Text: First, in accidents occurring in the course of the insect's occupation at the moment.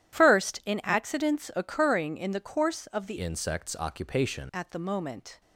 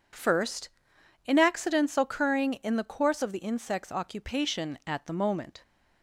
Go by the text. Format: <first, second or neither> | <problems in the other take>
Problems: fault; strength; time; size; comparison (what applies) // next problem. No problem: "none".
second | changes voice from "insect's" to "occupation"; from 3.1 to 4.4 s; 1.3 s long